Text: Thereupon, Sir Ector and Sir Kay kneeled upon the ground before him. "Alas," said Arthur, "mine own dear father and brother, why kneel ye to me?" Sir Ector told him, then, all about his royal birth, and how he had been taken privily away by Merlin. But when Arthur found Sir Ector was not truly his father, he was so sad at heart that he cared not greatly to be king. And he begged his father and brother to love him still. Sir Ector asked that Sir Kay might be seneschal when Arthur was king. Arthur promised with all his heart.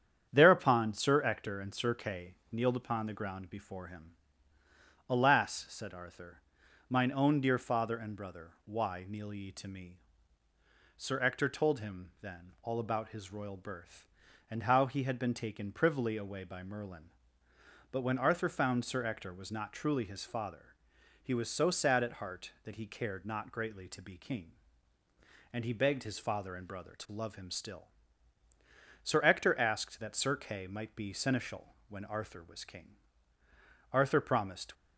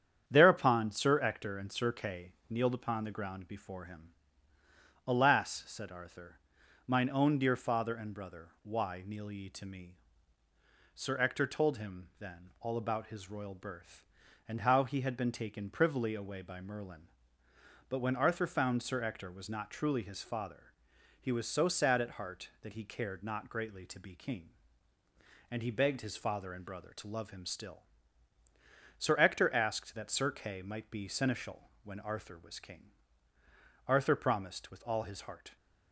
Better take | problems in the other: second | starts louder than the rest; strong; until 1.3 s; 8.5 dB; strong in the second // pauses between "Kay" and "kneeled"; slight; at 2.3 s; 0.18 s long; slight in the second // pauses between "seneschal" and "when"; slight; at 31.7 s; 0.16 s long; slight in the second // stops before "with all his heart"; at 34.7 s

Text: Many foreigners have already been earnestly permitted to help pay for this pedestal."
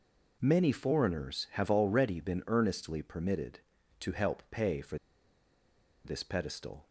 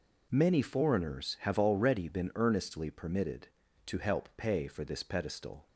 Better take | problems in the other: second | pauses between "for" and "this"; at 4.9 s; 1.0 s long

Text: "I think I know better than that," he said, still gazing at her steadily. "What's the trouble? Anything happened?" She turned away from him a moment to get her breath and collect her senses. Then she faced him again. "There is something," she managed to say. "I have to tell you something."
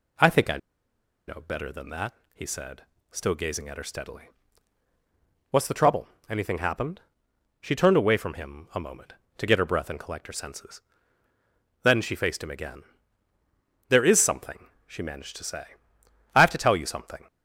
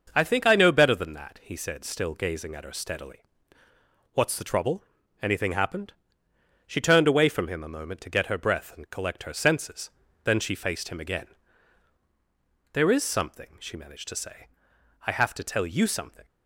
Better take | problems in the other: second | pauses between "I" and "know"; noticeable; at 0.5 s; 0.69 s long

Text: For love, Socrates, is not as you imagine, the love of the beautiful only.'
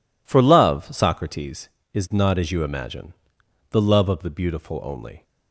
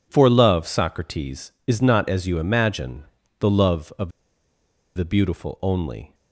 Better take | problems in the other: first | pauses between "of" and "the"; noticeable; at 4.0 s; 0.86 s long

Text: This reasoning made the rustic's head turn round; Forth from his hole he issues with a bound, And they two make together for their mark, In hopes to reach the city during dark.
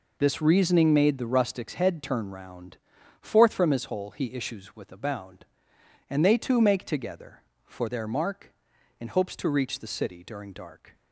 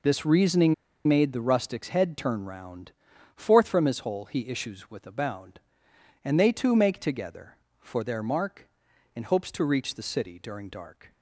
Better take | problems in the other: first | pauses between "reasoning" and "made"; slight; at 0.7 s; 0.33 s long

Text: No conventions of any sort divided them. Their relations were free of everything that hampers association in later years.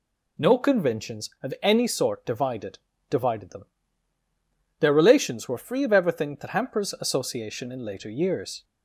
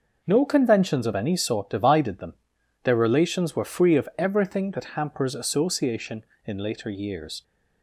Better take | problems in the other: second | says "divided" twice; at 3.0 s

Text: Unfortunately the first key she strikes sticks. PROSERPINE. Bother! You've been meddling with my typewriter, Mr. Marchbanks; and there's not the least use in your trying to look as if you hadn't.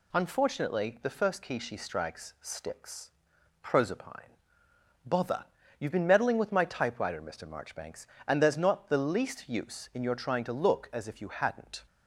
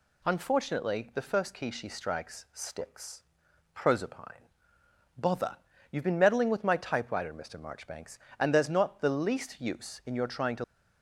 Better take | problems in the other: first | stops before "look as if you hadn't"; at 10.6 s

